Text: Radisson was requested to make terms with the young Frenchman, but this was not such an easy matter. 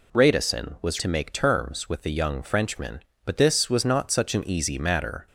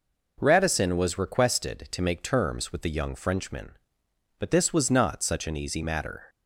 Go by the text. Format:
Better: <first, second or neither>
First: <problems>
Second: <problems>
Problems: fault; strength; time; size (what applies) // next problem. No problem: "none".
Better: second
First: skips "requested"; at 0.9 s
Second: none